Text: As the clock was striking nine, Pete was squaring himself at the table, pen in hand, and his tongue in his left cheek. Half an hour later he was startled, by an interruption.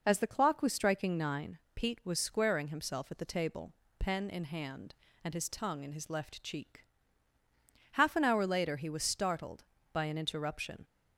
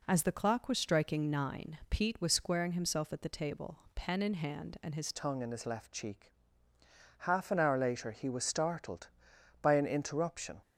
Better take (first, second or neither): first